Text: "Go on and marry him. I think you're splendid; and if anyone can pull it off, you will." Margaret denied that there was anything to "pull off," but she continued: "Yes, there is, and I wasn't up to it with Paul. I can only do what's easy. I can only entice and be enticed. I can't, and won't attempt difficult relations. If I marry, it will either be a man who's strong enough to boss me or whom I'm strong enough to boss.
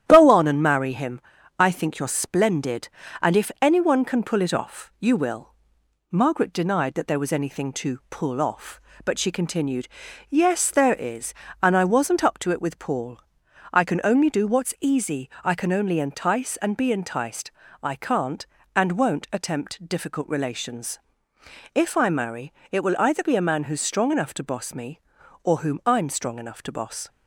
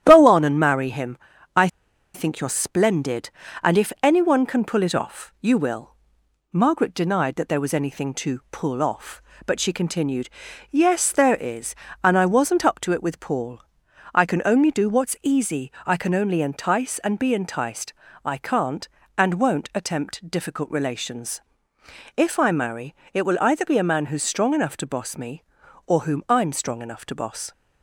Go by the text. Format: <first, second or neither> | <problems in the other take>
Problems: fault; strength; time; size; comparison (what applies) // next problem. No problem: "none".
first | starts louder than the rest; strong; until 1.0 s; 11 dB; strong in the first // pauses between "I" and "think"; noticeable; at 1.6 s; 0.47 s long